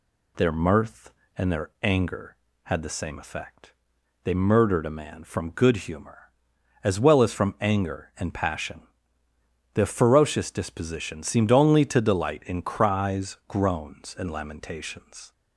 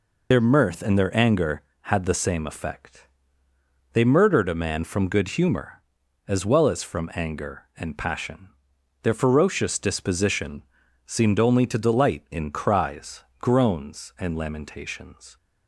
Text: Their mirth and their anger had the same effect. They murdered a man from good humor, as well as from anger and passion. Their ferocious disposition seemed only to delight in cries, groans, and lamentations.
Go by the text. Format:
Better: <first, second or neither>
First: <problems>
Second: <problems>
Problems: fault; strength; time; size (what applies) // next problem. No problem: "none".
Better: first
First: none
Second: loses the start of "Their"; at 0.3 s; 60 ms // pauses between "disposition" and "seemed"; at 10.6 s; 0.42 s long